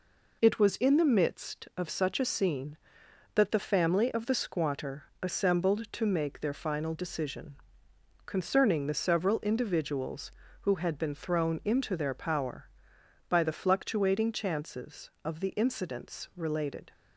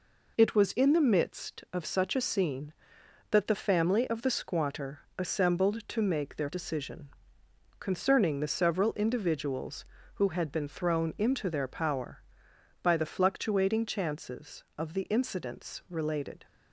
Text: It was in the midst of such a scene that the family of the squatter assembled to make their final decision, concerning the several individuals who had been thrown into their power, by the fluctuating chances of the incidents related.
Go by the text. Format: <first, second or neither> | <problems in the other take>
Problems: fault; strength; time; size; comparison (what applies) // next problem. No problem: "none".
first | pauses between "squatter" and "assembled"; slight; at 4.9 s; 0.20 s long; slight in the first // skips "final"; at 6.4 s